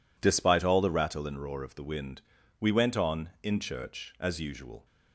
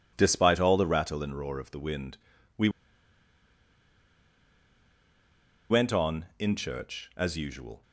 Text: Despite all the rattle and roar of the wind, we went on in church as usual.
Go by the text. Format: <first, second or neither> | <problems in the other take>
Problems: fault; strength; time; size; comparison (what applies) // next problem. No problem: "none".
first | pauses between "we" and "went"; strong; at 2.6 s; 3.0 s long